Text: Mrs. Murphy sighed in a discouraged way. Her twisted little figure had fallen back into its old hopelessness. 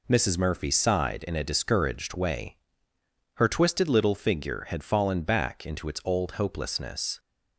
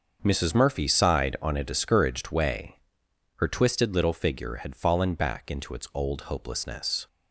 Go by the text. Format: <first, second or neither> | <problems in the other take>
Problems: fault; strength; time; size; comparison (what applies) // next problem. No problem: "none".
first | starts louder than the rest; until 1.2 s; 6.5 dB // says "on" for "in"; at 1.4 s